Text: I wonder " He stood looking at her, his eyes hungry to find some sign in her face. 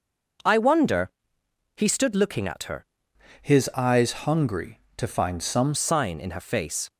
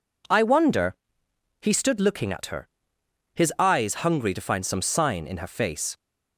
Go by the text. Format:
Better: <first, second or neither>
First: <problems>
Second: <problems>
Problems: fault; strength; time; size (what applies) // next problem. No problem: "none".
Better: second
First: changes voice from "his" to "some"; from 3.4 to 5.7 s; 2.3 s long // pauses between "eyes" and "hungry"; slight; at 4.1 s; 0.18 s long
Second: none